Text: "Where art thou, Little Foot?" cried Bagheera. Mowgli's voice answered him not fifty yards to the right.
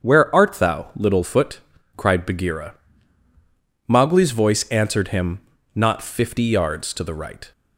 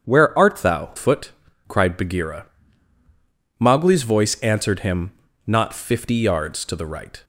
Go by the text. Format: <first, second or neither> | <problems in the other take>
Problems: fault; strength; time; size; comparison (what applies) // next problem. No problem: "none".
first | starts louder than the rest; strong; until 1.0 s; 7.5 dB; strong in the first // skips "Little"; at 0.9 s // pauses between "him" and "not"; at 5.0 s; 0.38 s long; also in the first